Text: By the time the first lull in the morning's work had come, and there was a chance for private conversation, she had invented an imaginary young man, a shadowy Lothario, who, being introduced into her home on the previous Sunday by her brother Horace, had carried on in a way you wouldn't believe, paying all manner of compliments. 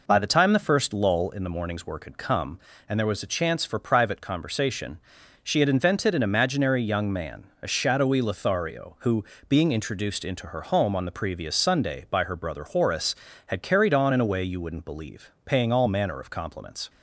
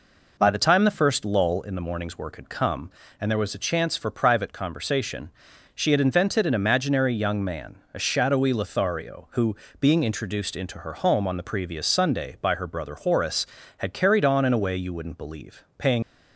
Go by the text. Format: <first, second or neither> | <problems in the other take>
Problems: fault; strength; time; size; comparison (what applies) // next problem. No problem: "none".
first | stops before "all manner of compliments"; at 16.0 s